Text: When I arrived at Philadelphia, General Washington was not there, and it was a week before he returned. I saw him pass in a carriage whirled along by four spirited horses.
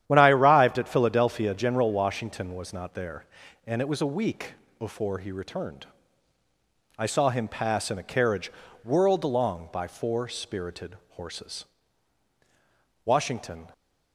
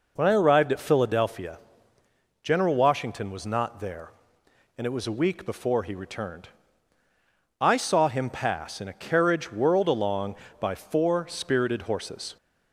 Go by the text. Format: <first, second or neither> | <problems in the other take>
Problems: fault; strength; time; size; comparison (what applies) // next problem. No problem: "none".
second | starts louder than the rest; strong; until 1.0 s; 10 dB // pauses between "week" and "before"; slight; at 4.5 s; 0.26 s long // pauses between "carriage" and "whirled"; slight; at 8.5 s; 0.34 s long // goes on to say "Washington"; noticeable; from 13.0 s on; 0.62 s long